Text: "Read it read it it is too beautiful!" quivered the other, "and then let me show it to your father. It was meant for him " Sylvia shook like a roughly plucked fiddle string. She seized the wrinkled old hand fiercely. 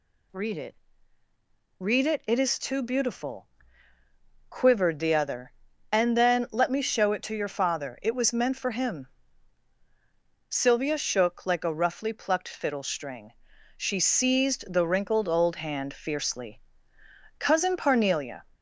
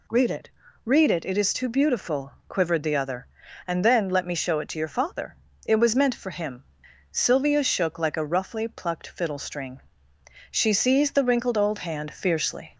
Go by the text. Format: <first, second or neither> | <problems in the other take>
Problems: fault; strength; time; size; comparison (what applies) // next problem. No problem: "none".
second | pauses between "it" and "read"; at 0.7 s; 1.0 s long; slight in the second // goes on to say "Cousin Parnelia"; noticeable; from 17.3 s on; 1.0 s long